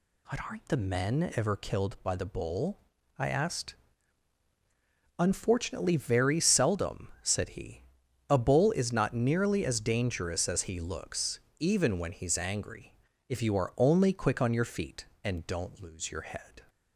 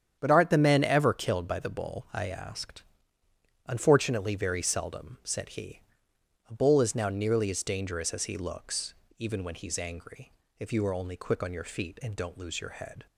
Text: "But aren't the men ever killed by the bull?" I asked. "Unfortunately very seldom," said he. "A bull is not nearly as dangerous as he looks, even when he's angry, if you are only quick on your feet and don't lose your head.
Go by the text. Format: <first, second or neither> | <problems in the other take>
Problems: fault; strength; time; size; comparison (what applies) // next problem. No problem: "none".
first | starts louder than the rest; strong; until 1.2 s; 8.5 dB // says "now" for "not"; at 6.9 s